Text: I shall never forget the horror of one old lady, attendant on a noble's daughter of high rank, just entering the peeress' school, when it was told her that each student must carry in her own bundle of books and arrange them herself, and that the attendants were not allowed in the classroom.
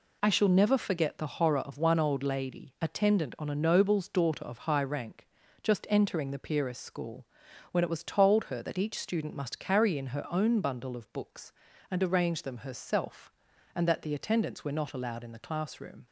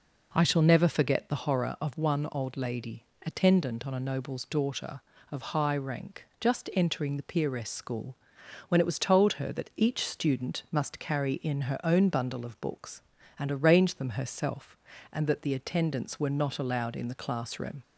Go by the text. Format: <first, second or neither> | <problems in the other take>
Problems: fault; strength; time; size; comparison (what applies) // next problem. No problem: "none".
neither | none